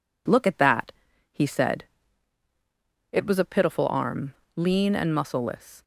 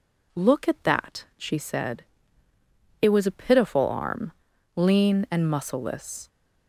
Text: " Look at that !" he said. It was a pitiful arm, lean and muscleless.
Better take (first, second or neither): first